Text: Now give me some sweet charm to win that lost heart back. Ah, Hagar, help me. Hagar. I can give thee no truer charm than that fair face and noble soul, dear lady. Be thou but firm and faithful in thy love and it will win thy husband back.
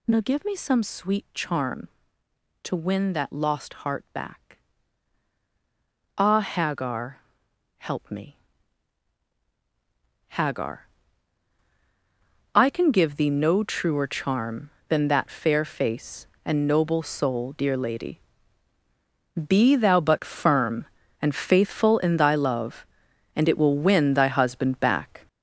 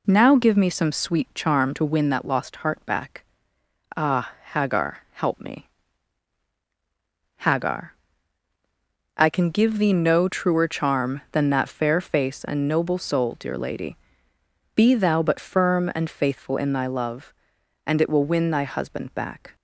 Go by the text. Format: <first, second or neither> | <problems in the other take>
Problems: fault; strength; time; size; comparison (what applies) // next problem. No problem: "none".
second | gets louder; strong; throughout; 7.5 dB